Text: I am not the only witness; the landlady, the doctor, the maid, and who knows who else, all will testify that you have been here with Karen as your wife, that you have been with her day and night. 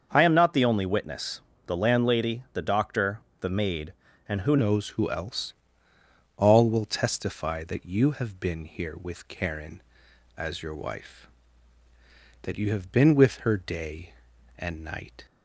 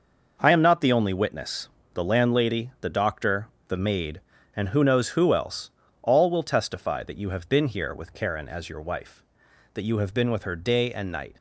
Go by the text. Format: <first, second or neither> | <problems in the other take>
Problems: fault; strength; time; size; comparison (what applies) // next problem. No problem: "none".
second | starts louder than the rest; until 1.1 s; 6.5 dB // changes voice at "knows"; from 4.5 s on; 10.7 s long